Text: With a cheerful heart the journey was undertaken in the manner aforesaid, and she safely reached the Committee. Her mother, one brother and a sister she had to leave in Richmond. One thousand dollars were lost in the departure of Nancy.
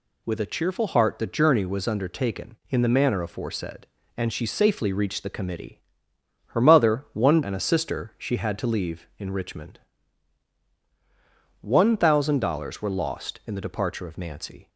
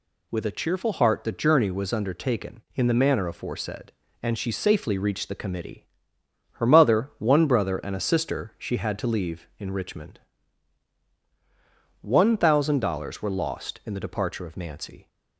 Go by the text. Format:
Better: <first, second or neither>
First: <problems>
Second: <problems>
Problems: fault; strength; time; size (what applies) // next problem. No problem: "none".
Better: second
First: skips "brother"; at 7.4 s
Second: none